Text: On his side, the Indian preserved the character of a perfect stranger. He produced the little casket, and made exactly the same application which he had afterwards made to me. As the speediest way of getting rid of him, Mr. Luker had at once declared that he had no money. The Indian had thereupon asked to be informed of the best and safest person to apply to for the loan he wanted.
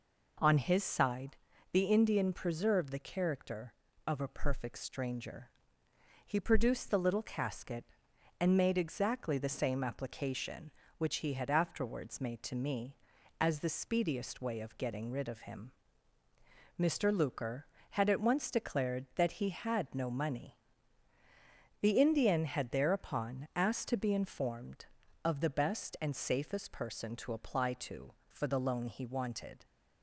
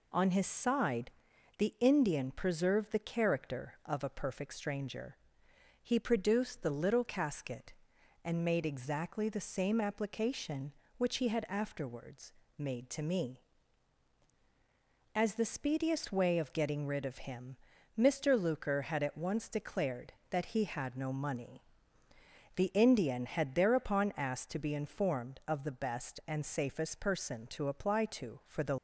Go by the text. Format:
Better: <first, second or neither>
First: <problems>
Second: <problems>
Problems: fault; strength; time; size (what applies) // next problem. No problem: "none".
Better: first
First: none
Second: pauses between "afterwards" and "made"; slight; at 12.3 s; 0.24 s long // stops before "loan he wanted"; at 28.7 s